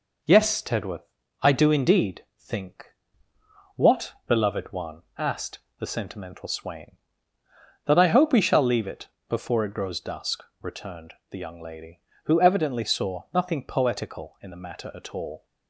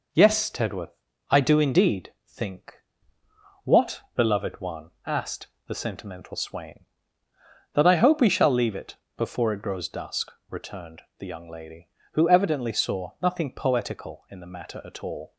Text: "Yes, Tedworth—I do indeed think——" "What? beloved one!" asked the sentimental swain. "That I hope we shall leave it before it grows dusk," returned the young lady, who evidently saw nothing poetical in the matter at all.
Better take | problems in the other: neither | pauses between "asked" and "the"; slight; the same in both // pauses between "it" and "before"; slight; the same in both // pauses between "returned" and "the"; slight; the same in both

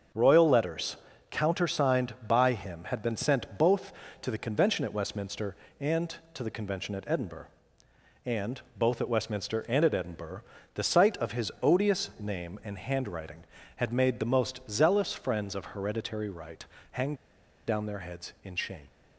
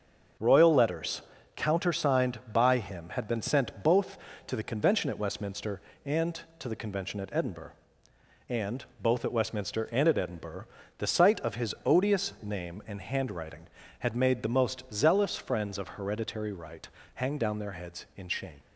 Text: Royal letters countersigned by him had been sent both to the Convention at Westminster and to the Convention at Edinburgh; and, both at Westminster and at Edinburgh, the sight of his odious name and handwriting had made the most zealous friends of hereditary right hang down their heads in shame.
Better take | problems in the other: second | starts louder than the rest; until 1.4 s; 7 dB; also in the second // pauses between "letters" and "countersigned"; slight; at 0.9 s; 0.34 s long; slight in the second // pauses between "right" and "hang"; slight; at 16.6 s; 0.26 s long; slight in the second // pauses between "hang" and "down"; noticeable; at 17.1 s; 0.52 s long

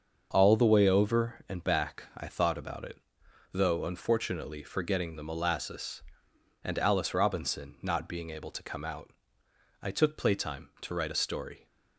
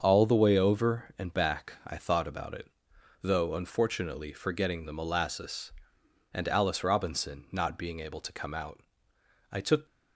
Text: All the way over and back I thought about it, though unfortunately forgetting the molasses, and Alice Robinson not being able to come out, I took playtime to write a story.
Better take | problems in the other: first | starts louder than the rest; until 1.0 s; 6.5 dB; also in the first // stops before "playtime to write a story"; at 9.8 s

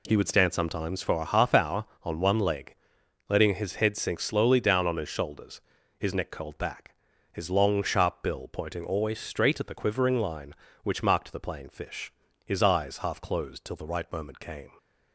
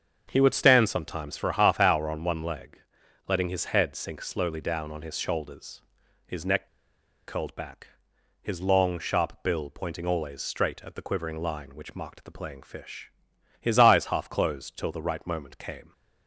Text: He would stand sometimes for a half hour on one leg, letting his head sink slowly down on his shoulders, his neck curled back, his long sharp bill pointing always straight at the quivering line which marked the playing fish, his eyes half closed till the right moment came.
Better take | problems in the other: first | starts louder than the rest; strong; until 1.3 s; 7 dB // pauses between "neck" and "curled"; noticeable; at 6.6 s; 0.60 s long

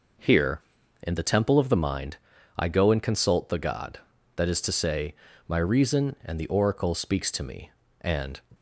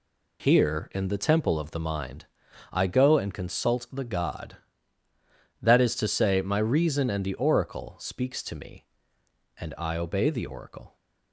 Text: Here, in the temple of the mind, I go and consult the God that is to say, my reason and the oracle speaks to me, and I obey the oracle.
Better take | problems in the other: second | stops before "I obey the oracle"; at 8.5 s

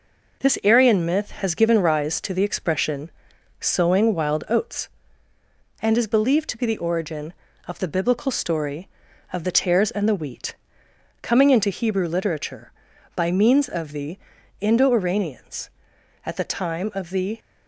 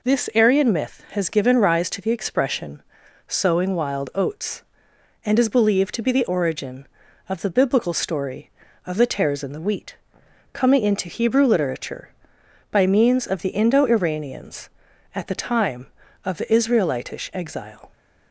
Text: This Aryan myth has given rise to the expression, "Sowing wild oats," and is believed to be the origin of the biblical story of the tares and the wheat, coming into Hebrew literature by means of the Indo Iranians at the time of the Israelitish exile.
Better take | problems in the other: second | pauses between "the" and "Indo"; at 14.1 s; 0.40 s long // stops before "Israelitish exile"; at 17.3 s

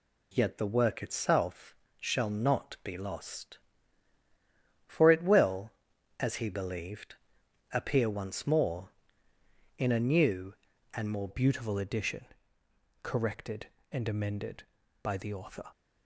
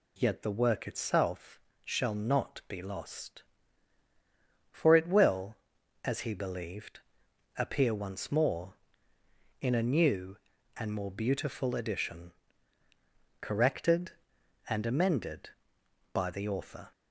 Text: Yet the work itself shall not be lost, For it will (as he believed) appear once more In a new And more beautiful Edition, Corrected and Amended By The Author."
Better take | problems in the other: second | pauses between "itself" and "shall"; slight; at 1.7 s; 0.26 s long; slight in the second // changes voice at "beautiful"; from 11.2 s on; 4.5 s long

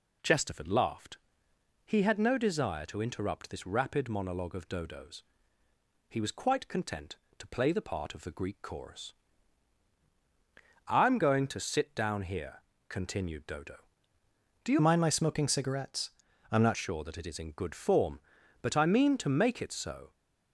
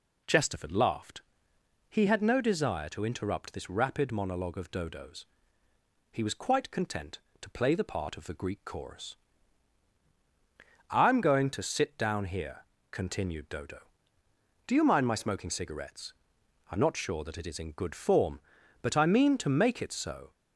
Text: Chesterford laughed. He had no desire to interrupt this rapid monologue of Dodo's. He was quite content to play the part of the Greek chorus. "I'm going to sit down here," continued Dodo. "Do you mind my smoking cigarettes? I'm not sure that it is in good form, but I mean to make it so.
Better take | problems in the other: second | changes voice from "mind" to "not"; from 14.7 to 16.7 s; 2.0 s long

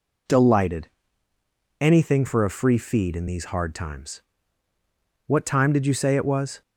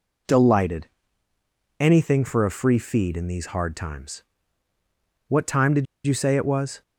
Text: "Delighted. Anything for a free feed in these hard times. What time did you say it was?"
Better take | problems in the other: first | pauses between "did" and "you"; slight; at 5.8 s; 0.20 s long

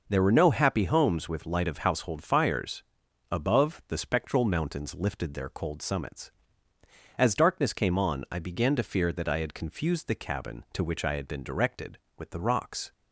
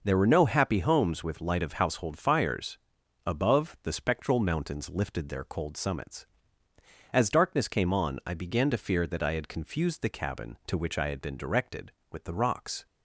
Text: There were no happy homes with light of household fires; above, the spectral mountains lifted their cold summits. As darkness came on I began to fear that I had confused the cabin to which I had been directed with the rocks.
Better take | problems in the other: neither | none

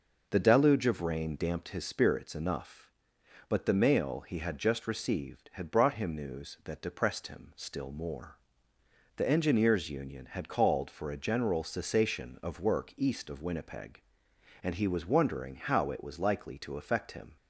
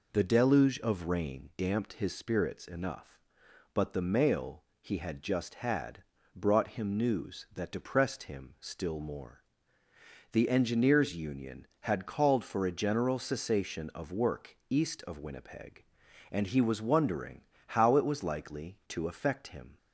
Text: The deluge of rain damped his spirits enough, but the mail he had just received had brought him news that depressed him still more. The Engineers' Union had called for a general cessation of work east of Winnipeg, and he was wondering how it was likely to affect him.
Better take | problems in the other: first | pauses between "mail" and "he"; slight; at 4.6 s; 0.18 s long // skips "received"; at 5.5 s // pauses between "had" and "brought"; slight; at 6.0 s; 0.32 s long // pauses between "wondering" and "how"; slight; at 17.4 s; 0.24 s long

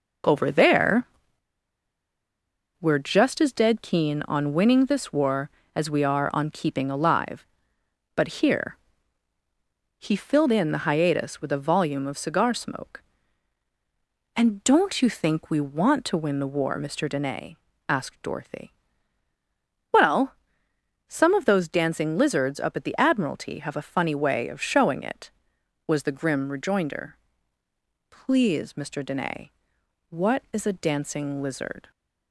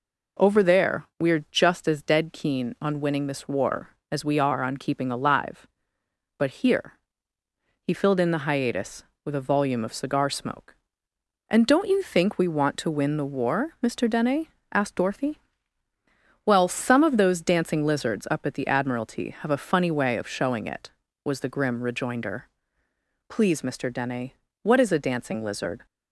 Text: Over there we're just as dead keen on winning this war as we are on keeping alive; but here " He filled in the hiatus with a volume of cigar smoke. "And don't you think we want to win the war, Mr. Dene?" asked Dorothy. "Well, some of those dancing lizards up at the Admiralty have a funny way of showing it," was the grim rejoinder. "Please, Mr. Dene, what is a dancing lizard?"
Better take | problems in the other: second | pauses between "there" and "we're"; strong; at 1.0 s; 1.7 s long

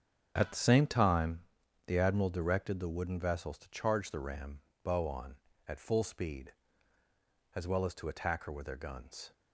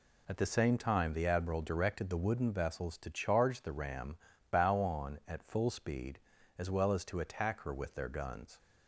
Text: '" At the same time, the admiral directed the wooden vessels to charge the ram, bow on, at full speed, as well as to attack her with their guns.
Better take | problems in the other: second | gets quieter; strong; throughout; 10.5 dB

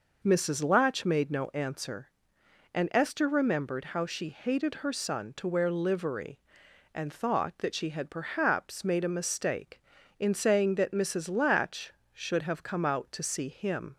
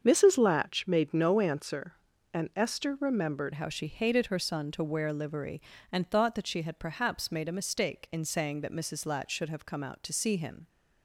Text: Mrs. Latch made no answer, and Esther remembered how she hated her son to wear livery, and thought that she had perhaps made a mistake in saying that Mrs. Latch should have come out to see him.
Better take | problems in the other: first | starts louder than the rest; until 1.0 s; 7 dB // changes voice at "how"; from 3.5 s on; 7.1 s long

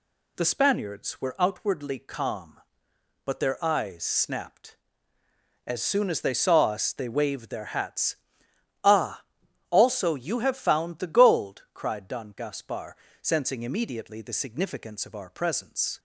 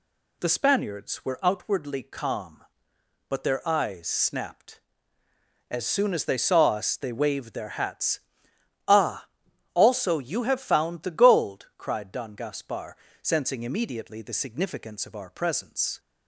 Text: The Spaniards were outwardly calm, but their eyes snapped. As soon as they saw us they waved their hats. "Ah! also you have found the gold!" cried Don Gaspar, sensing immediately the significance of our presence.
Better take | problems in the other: neither | none

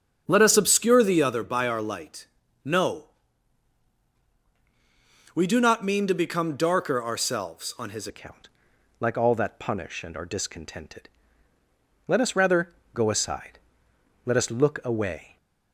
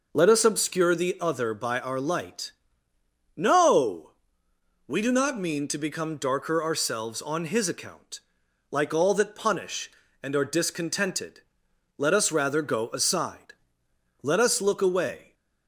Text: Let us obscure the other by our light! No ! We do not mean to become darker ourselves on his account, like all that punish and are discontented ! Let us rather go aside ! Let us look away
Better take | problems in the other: second | starts louder than the rest; strong; until 1.2 s; 8 dB // changes voice at "account"; from 8.0 s on; 7.3 s long // pauses between "rather" and "go"; slight; at 12.7 s; 0.20 s long

